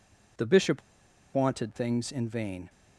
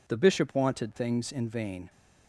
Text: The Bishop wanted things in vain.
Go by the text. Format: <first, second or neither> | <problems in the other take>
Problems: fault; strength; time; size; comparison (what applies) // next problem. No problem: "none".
second | pauses between "Bishop" and "wanted"; noticeable; at 0.8 s; 0.54 s long